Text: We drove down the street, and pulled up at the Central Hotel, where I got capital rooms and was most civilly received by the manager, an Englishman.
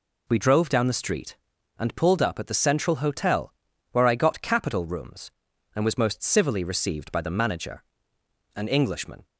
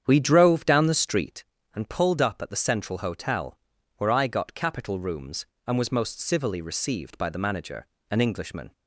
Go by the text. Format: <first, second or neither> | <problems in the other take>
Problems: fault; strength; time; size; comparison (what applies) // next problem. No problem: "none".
first | starts louder than the rest; strong; until 1.4 s; 8.5 dB